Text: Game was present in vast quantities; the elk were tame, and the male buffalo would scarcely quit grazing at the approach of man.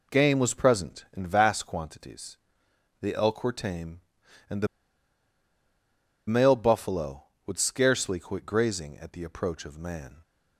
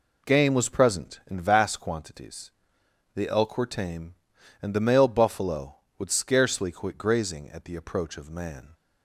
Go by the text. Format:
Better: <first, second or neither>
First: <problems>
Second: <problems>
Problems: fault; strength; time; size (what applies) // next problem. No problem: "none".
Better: second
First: pauses between "the" and "male"; strong; at 4.6 s; 1.6 s long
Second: none